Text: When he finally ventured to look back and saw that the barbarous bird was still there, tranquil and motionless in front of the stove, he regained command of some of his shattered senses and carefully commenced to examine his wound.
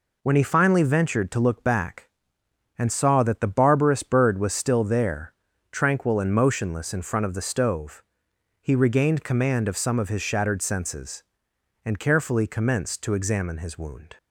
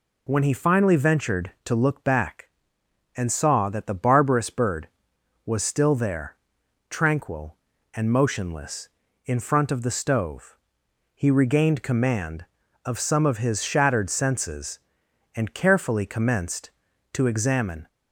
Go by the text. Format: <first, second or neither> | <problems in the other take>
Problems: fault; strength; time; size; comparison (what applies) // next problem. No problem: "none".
first | stops before "his wound"; at 17.8 s